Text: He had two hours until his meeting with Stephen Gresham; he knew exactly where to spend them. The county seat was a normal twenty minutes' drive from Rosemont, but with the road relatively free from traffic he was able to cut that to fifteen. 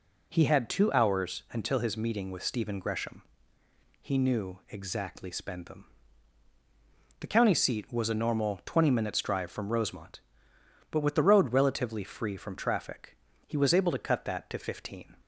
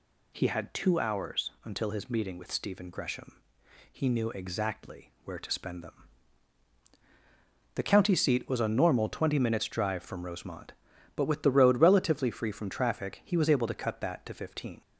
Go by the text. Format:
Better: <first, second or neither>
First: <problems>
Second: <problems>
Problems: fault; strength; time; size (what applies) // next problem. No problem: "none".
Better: second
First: skips "where to"; at 5.3 s // pauses between "traffic" and "he"; slight; at 13.1 s; 0.30 s long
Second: none